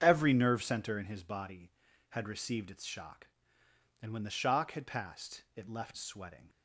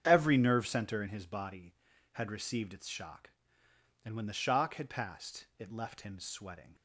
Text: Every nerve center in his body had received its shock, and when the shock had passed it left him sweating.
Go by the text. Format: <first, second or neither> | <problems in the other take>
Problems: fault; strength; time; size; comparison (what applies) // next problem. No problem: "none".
second | starts louder than the rest; strong; until 1.0 s; 7.5 dB; strong in the second // skips "him"; at 5.9 s